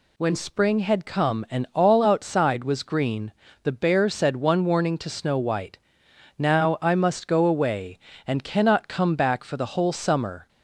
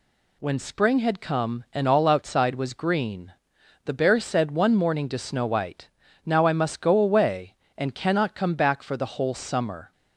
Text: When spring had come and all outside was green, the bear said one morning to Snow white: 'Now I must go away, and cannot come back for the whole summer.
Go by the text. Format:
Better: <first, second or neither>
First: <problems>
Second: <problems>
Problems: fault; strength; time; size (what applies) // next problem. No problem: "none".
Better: second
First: says "warning" for "morning"; at 4.6 s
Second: none